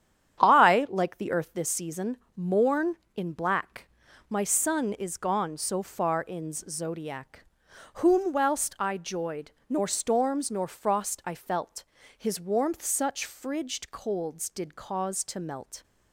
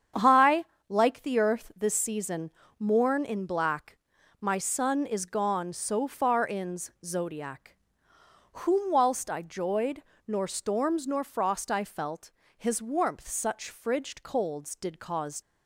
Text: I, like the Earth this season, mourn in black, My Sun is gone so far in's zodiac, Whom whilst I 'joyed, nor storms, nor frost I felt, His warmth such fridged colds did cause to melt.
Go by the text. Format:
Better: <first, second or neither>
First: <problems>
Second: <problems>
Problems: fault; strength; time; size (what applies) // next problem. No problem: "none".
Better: first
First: starts louder than the rest; strong; until 1.4 s; 9.5 dB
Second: starts louder than the rest; strong; until 1.4 s; 8 dB // stops before "to melt"; at 15.4 s